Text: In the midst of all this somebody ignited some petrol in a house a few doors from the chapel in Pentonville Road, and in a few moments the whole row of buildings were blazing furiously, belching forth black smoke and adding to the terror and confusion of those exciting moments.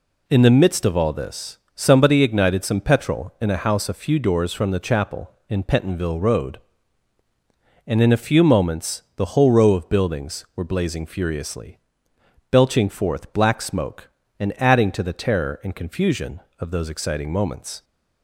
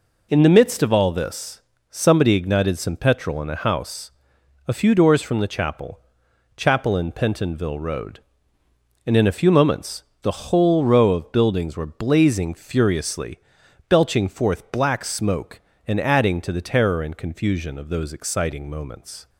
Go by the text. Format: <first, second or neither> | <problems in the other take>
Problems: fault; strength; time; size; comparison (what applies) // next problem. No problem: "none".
first | pauses between "this" and "somebody"; slight; at 1.6 s; 0.26 s long; slight in the first // pauses between "house" and "a"; noticeable; at 4.1 s; 0.56 s long // says "chapel" twice; at 6.5 s // pauses between "moments" and "the"; slight; at 10.0 s; 0.18 s long